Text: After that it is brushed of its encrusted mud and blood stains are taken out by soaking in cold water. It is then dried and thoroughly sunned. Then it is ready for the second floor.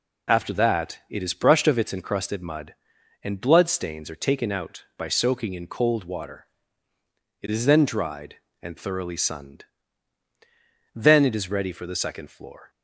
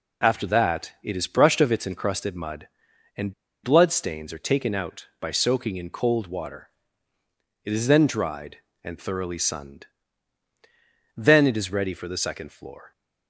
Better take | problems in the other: first | pauses between "and" and "blood"; slight; at 3.3 s; 0.29 s long

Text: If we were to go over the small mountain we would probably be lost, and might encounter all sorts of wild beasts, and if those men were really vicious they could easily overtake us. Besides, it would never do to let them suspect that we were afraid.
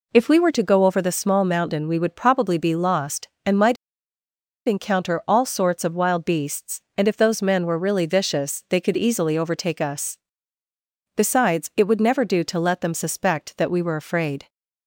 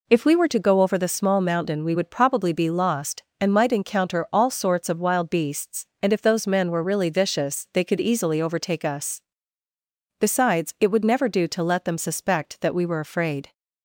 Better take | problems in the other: second | pauses between "might" and "encounter"; noticeable; at 3.7 s; 0.90 s long

